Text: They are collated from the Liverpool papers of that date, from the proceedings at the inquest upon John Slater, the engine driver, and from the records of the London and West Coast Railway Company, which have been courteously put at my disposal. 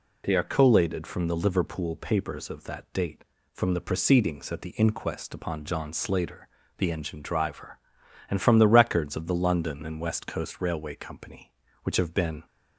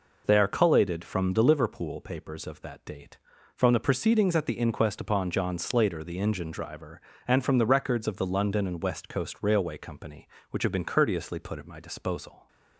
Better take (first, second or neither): second